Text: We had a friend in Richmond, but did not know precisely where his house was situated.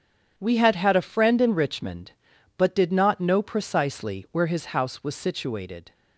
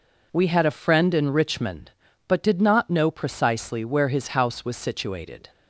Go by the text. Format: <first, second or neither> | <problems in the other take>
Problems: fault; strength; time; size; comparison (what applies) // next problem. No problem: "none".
second | starts louder than the rest; strong; until 1.3 s; 9 dB // says "had" twice; at 0.7 s